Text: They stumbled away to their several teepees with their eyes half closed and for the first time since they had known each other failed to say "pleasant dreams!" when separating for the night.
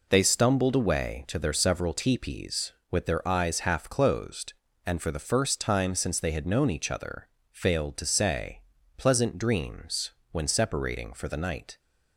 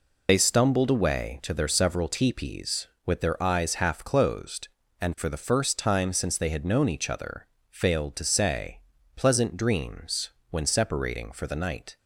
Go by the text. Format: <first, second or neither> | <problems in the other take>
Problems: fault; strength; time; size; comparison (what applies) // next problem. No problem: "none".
first | loses the start of "They"; at 0.2 s; 45 ms // pauses between "other" and "failed"; slight; at 7.4 s; 0.24 s long; slight in the first // pauses between "say" and "pleasant"; slight; at 8.7 s; 0.36 s long; slight in the first